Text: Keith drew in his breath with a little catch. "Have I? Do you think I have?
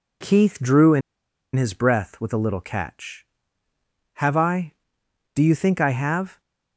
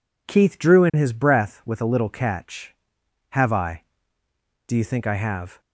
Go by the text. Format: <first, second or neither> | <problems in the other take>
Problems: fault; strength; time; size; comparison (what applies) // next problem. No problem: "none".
second | pauses between "in" and "his"; noticeable; at 1.0 s; 0.54 s long